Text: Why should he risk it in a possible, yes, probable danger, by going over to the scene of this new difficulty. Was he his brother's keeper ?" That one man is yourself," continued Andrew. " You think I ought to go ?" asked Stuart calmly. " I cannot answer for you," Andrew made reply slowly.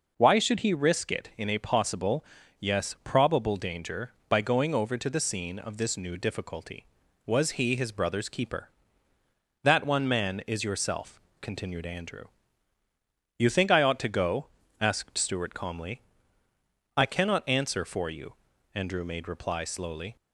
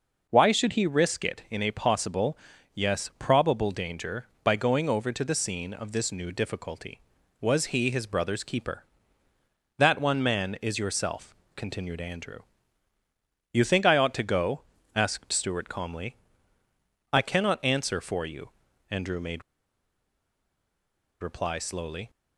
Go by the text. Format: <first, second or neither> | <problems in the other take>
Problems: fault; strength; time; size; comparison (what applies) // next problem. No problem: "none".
first | pauses between "made" and "reply"; strong; at 19.4 s; 1.7 s long